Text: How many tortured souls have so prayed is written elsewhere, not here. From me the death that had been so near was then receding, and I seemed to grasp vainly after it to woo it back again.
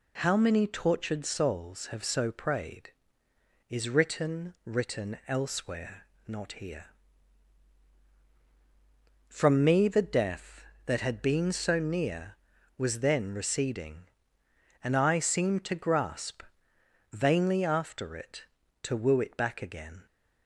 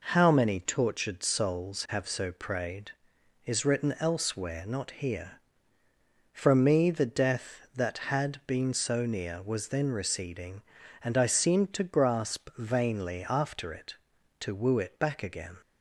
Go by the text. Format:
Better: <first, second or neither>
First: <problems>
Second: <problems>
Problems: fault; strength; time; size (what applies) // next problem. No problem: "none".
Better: second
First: says "written" twice; at 4.6 s // pauses between "grasp" and "vainly"; noticeable; at 16.4 s; 0.70 s long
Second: none